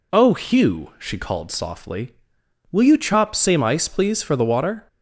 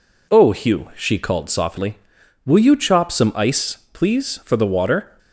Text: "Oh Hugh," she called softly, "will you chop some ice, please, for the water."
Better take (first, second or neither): second